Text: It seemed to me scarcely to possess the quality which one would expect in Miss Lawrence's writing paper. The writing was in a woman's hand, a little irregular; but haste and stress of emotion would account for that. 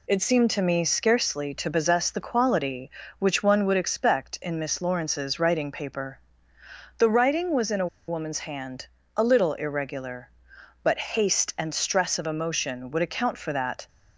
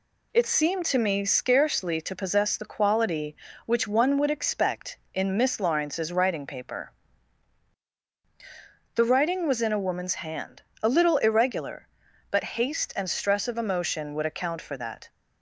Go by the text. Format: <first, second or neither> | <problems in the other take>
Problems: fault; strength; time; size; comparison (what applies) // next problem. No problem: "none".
second | pauses between "a" and "woman's"; slight; at 7.8 s; 0.22 s long